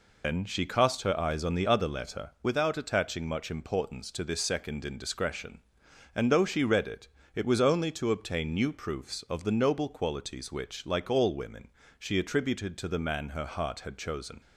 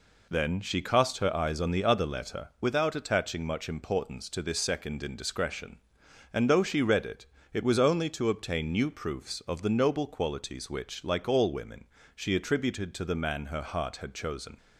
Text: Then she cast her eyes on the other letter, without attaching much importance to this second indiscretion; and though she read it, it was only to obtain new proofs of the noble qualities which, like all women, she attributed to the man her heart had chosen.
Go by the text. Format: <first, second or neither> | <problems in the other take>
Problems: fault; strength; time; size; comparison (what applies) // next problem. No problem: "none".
second | loses the start of "Then"; at 0.2 s; 105 ms